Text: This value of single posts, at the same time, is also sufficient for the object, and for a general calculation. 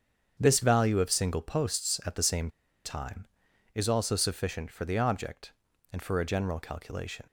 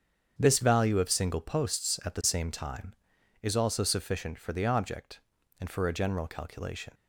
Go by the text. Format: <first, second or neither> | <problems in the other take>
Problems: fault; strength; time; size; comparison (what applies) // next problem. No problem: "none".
second | starts louder than the rest; strong; until 1.4 s; 8 dB; strong in the second // pauses between "same" and "time"; at 2.4 s; 0.36 s long